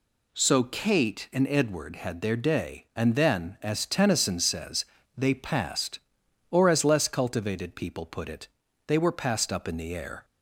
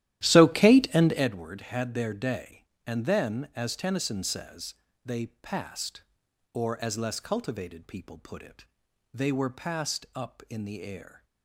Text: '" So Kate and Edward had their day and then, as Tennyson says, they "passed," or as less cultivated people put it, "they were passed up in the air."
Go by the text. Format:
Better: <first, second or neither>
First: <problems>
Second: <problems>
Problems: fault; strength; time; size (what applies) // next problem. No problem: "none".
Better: first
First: none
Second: starts louder than the rest; strong; until 1.3 s; 13 dB